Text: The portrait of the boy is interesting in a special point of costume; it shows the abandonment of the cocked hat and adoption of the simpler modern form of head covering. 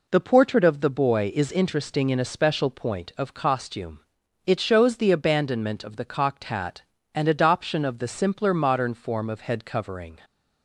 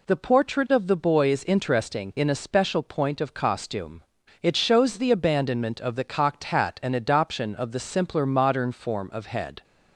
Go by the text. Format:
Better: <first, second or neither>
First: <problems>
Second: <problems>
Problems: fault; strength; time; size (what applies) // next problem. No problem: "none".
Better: first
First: none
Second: stops before "covering"; at 9.6 s